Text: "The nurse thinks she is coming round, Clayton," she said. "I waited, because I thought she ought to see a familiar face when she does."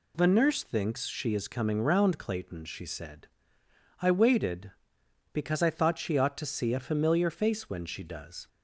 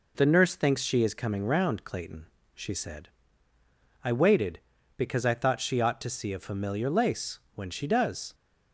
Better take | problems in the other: first | says "lace" for "face"; at 6.8 s

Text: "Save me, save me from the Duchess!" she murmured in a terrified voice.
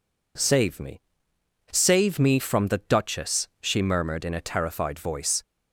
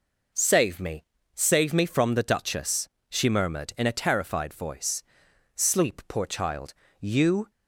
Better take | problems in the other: first | goes on to say "Sleep poor child you"; strong; from 5.5 s on; 1.9 s long

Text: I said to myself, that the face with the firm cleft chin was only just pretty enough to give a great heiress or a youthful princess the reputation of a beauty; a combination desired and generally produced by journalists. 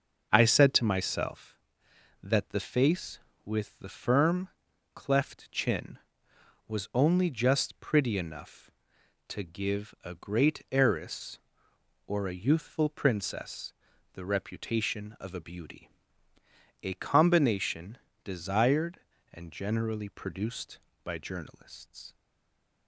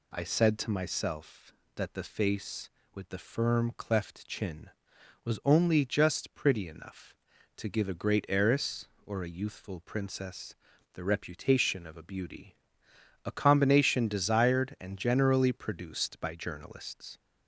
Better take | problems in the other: second | starts louder than the rest; until 1.3 s; 6.5 dB // pauses between "firm" and "cleft"; noticeable; at 4.4 s; 0.46 s long // pauses between "princess" and "the"; at 13.7 s; 0.42 s long; also in the second // pauses between "combination" and "desired"; slight; at 17.9 s; 0.28 s long // stays silent after the last word; slight; from 22.1 s on; 0.7 s long

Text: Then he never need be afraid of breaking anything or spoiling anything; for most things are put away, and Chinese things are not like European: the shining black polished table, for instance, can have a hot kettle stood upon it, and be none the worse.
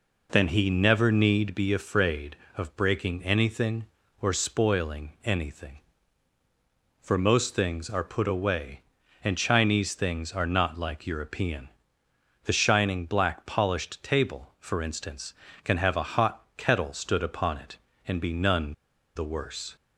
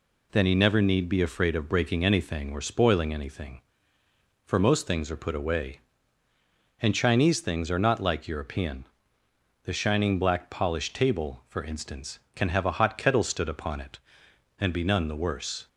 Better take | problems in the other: second | pauses between "none" and "the"; at 18.7 s; 0.41 s long

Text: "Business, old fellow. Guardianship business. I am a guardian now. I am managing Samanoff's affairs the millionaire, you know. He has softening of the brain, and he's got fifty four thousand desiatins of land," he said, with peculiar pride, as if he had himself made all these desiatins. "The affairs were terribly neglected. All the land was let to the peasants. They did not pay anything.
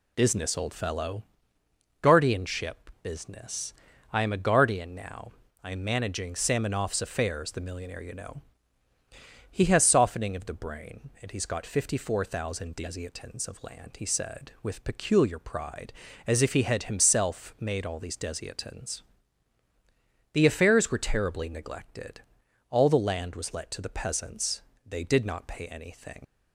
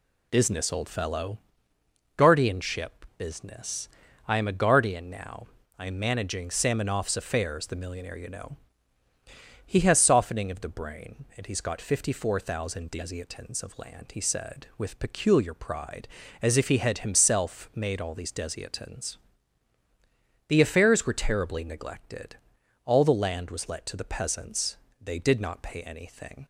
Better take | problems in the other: second | leaves "anything" unfinished; at 26.2 s; 50 ms

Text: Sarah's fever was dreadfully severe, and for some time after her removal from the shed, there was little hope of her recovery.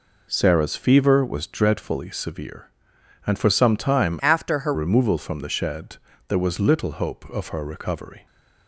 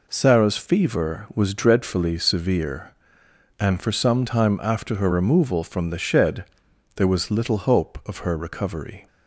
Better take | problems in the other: second | changes voice from "after" to "her"; from 4.1 to 4.7 s; 0.6 s long

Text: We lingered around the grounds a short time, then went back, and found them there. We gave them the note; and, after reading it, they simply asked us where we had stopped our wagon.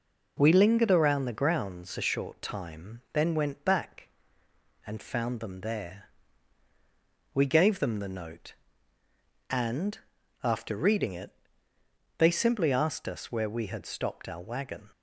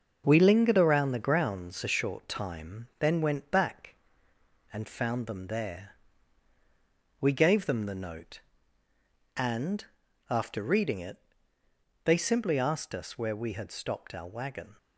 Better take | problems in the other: first | gets quieter; noticeable; throughout; 5.5 dB

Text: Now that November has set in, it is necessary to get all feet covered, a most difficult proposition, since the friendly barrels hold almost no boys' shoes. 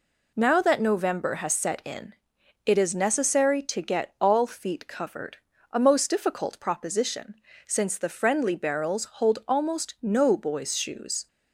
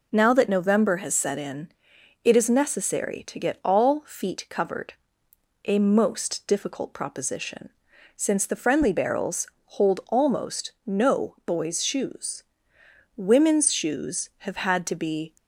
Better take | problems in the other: first | pauses between "barrels" and "hold"; slight; at 9.4 s; 0.18 s long // goes on to say "Women's shoes have had to be"; strong; from 13.1 s on; 2.2 s long

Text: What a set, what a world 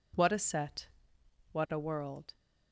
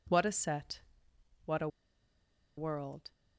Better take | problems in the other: first | pauses between "a" and "world"; noticeable; at 1.6 s; 0.89 s long

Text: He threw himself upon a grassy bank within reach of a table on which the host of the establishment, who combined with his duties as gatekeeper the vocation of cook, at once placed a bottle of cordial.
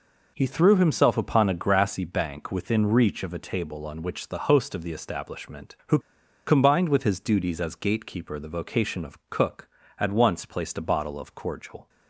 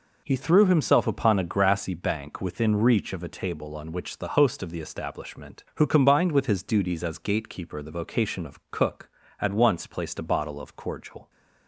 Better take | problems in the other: second | pauses between "who" and "combined"; noticeable; at 5.9 s; 0.46 s long

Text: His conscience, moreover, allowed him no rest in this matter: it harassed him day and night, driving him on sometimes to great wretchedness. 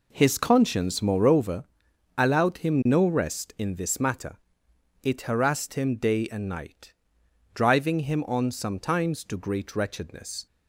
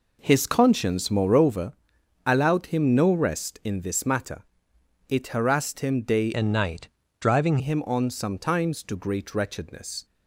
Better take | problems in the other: first | changes voice from "and" to "driving"; from 6.3 to 7.5 s; 1.2 s long

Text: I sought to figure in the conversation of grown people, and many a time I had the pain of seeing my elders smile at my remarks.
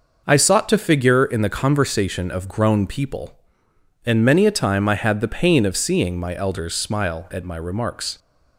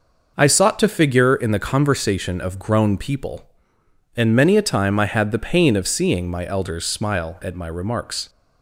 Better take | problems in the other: neither | none

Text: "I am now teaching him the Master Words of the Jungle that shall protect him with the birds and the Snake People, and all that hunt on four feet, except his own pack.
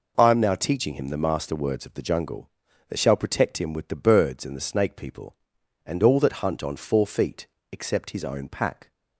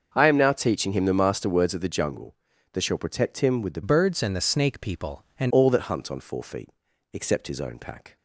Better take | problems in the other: first | starts louder than the rest; until 1.1 s; 6.5 dB // changes voice from "birds" to "and"; from 3.8 to 5.5 s; 1.7 s long

